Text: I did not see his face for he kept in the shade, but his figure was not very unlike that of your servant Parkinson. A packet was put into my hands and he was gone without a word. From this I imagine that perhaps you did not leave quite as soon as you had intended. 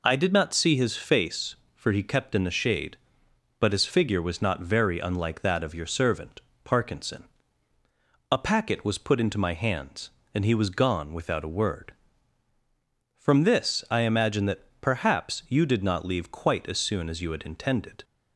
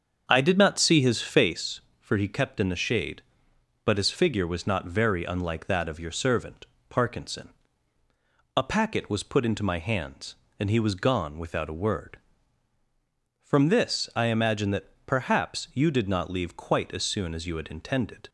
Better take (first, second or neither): first